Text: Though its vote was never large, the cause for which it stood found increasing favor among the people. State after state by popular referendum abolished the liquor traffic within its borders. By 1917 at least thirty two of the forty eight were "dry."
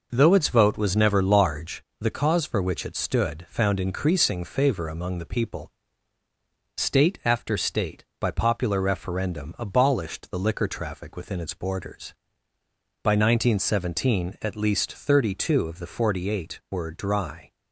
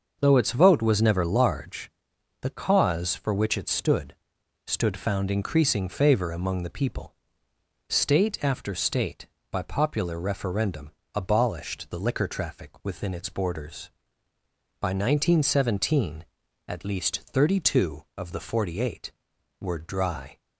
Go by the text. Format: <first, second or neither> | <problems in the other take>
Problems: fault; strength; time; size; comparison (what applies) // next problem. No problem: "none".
first | starts louder than the rest; until 1.2 s; 6.5 dB // says "stood" twice; at 4.6 s // pauses between "referendum" and "abolished"; slight; at 10.9 s; 0.22 s long